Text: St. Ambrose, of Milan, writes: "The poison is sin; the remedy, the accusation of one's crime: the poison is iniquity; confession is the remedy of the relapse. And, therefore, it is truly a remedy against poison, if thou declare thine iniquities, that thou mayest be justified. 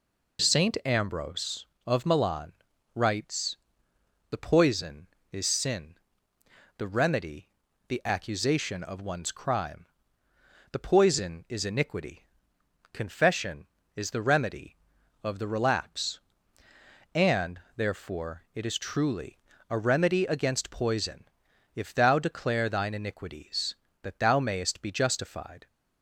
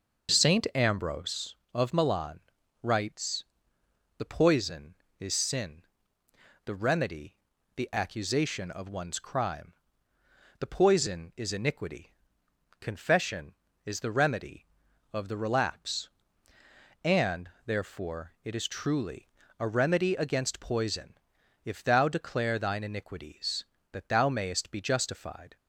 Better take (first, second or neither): first